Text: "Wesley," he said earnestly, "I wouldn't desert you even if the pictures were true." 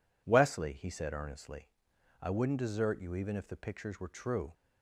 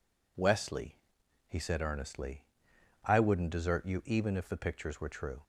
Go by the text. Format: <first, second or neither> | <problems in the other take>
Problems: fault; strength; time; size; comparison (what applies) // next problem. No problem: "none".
neither | none